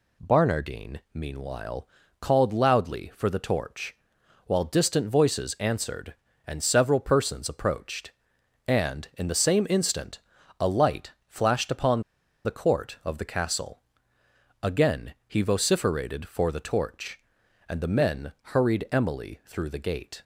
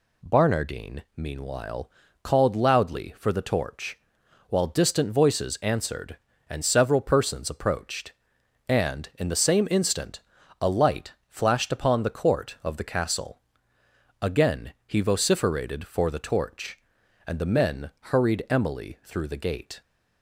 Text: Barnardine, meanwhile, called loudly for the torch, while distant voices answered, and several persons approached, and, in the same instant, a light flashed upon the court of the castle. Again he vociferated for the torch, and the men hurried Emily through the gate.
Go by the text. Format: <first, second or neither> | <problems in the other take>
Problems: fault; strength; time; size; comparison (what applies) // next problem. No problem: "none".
second | pauses between "light" and "flashed"; slight; at 11.1 s; 0.16 s long; slight in the second // pauses between "upon" and "the"; at 12.0 s; 0.44 s long